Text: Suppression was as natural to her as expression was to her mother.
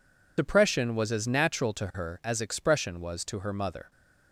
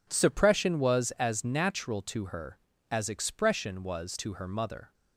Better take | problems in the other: second | loses the start of "Suppression"; at 0.3 s; 115 ms

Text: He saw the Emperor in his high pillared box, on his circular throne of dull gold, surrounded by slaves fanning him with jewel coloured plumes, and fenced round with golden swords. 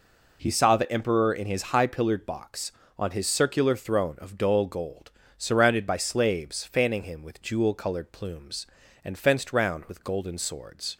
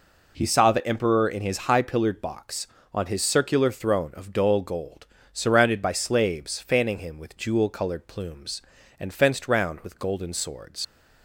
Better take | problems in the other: first | leaves "swords" unfinished; at 10.8 s; 70 ms

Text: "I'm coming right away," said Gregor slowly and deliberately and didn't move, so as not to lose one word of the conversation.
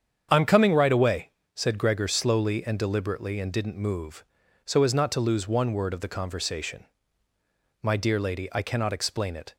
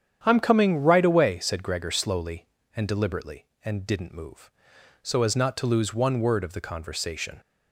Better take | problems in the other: second | starts louder than the rest; strong; until 1.3 s; 8 dB; strong in the second // goes on to say "My dear lady I cannot explain it"; strong; from 7.8 s on; 1.7 s long

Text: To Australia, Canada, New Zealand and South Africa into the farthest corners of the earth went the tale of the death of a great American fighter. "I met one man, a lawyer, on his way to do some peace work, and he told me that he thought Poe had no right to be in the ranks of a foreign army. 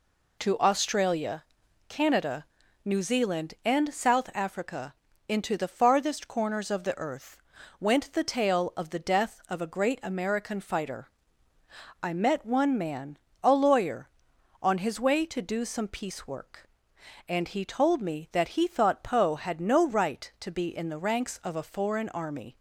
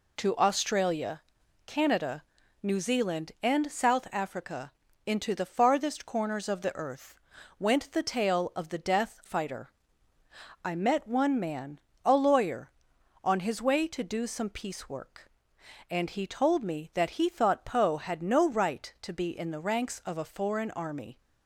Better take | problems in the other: first | pauses between "Africa" and "into"; slight; at 4.7 s; 0.34 s long; slight in the first // pauses between "earth" and "went"; at 7.1 s; 0.44 s long; also in the first // skips "of a great American"; at 9.2 s

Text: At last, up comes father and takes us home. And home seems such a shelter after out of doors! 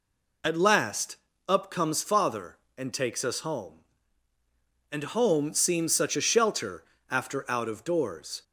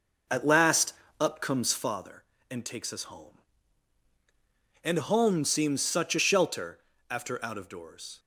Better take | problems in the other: first | starts louder than the rest; noticeable; until 2.0 s; 5.5 dB // pauses between "shelter" and "after"; slight; at 6.7 s; 0.30 s long; slight in the first

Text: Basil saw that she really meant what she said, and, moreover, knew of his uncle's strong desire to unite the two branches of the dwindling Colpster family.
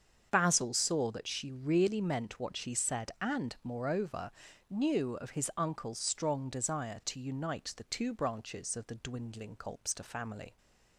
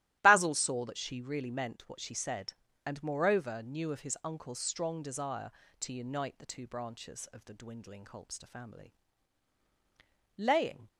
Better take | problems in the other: first | starts louder than the rest; strong; until 1.2 s; 15.5 dB; strong in the first // goes on to say "Laying"; from 10.3 s on; 0.52 s long

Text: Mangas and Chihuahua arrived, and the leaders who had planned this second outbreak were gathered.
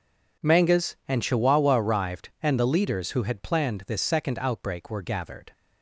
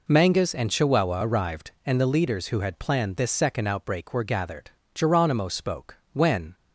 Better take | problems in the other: first | goes on to say "Geronimo spoke When"; from 4.9 s on; 1.6 s long

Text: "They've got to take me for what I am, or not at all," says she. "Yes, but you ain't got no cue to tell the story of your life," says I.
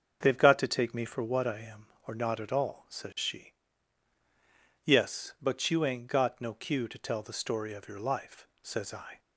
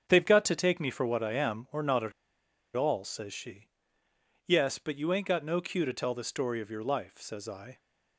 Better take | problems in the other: first | starts louder than the rest; strong; until 1.0 s; 7.5 dB; also in the first // pauses between "at" and "all"; noticeable; at 2.1 s; 0.63 s long

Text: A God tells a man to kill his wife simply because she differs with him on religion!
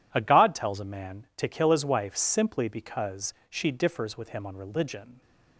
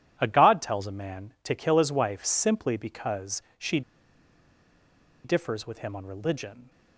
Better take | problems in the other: first | pauses between "because" and "she"; slight; at 3.4 s; 0.18 s long; slight in the first // pauses between "she" and "differs"; strong; at 3.8 s; 1.4 s long

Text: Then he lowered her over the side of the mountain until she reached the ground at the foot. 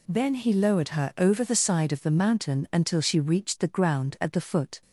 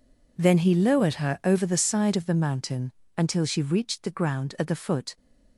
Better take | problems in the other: first | gets quieter; strong; throughout; 15 dB // pauses between "mountain" and "until"; slight; at 2.9 s; 0.24 s long

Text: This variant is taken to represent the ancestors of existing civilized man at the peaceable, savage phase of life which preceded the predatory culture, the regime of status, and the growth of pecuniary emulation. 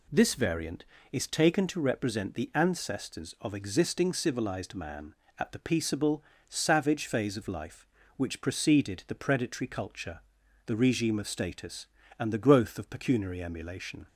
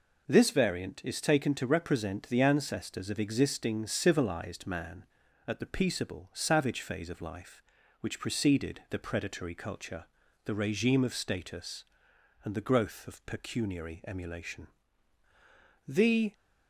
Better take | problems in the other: first | goes on to say "The"; slight; from 15.8 s on; 0.46 s long

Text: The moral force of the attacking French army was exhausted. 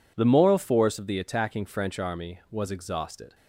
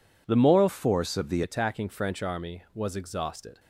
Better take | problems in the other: first | changes voice from "force" to "the"; from 0.6 to 1.4 s; 0.8 s long

